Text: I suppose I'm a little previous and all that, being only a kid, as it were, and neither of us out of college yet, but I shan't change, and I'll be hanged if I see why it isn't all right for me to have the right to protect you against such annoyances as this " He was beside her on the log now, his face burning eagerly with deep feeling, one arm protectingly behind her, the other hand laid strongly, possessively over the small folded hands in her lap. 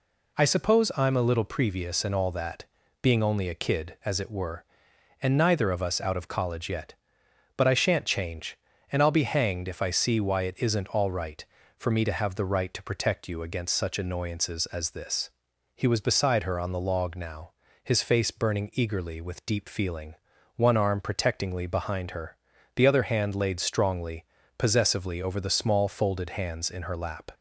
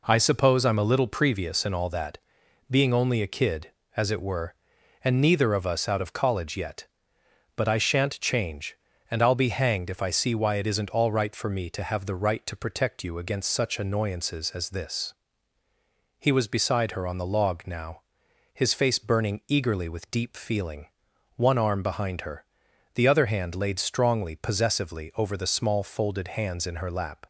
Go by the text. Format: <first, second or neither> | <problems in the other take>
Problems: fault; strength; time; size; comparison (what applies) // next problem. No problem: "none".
first | skips "protectingly"; at 21.8 s